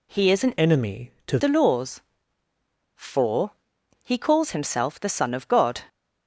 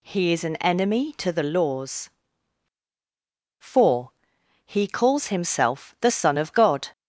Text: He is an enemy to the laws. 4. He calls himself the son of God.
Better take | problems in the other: second | changes voice from "enemy" to "to"; from 0.5 to 1.3 s; 0.8 s long

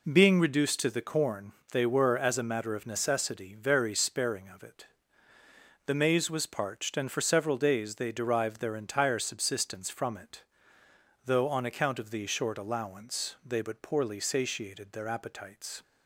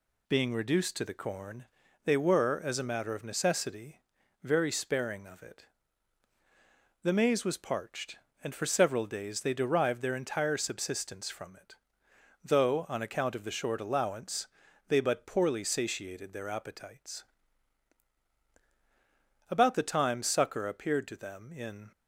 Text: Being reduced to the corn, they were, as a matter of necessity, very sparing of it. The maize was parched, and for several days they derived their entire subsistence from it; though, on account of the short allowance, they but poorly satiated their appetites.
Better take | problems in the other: first | goes on to say "About the time succor appeared to them in"; strong; from 19.4 s on; 2.4 s long

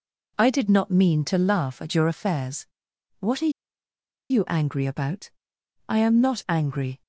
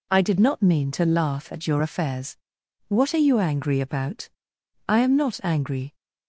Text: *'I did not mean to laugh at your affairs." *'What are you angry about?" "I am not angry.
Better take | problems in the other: second | pauses between "are" and "you"; noticeable; at 3.5 s; 0.79 s long

